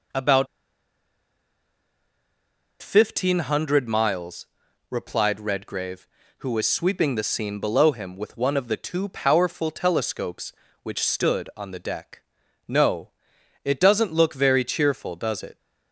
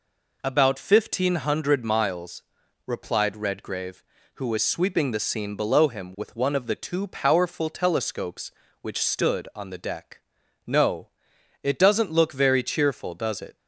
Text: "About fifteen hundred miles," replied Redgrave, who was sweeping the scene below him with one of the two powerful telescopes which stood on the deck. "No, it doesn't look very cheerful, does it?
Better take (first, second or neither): second